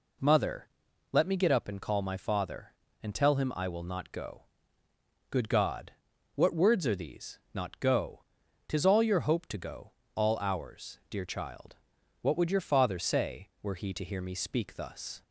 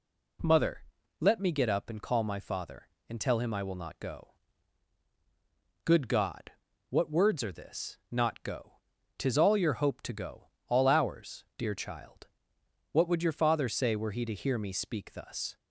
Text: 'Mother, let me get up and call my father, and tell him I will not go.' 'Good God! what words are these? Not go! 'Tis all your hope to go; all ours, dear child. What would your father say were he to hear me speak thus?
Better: first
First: none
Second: says "this" for "these"; at 7.5 s

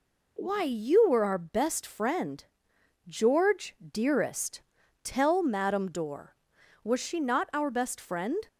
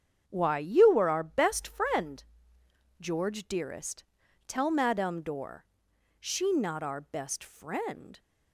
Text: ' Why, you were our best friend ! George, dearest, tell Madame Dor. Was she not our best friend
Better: first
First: none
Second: starts louder than the rest; strong; until 1.2 s; 8 dB // skips "Was"; at 5.9 s

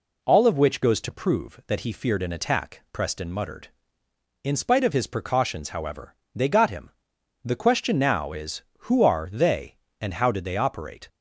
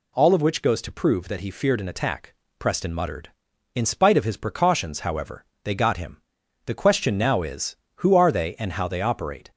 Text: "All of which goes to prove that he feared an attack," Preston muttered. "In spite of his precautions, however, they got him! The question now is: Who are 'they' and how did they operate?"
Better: first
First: none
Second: skips "did"; at 8.8 s

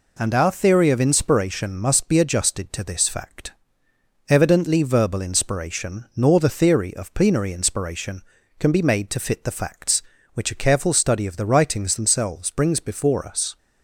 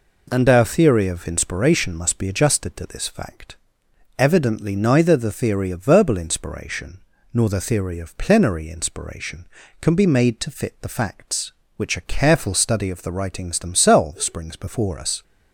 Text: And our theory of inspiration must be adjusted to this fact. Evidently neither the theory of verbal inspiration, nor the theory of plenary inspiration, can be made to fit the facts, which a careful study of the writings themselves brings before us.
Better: second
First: skips "neither the theory of"; at 4.8 s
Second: none

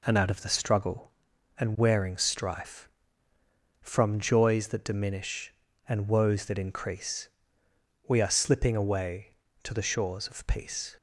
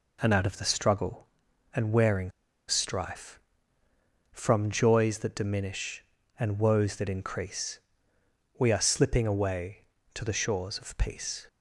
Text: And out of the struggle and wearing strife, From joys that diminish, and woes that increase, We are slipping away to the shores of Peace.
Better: first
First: none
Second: pauses between "wearing" and "strife"; at 2.2 s; 0.38 s long

